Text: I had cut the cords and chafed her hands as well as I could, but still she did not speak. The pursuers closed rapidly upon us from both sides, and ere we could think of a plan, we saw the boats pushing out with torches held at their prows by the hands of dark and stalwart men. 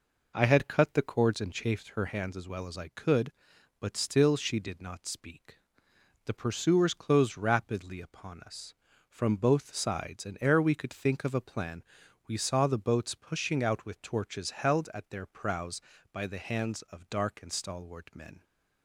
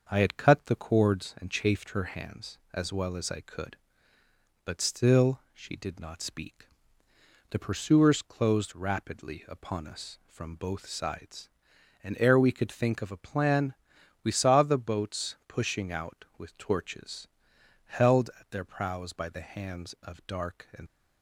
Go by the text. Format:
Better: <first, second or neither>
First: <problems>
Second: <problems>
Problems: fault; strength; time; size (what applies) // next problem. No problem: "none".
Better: first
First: none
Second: starts louder than the rest; until 1.1 s; 6.5 dB // pauses between "torches" and "held"; noticeable; at 17.2 s; 0.58 s long // stops before "stalwart men"; at 20.8 s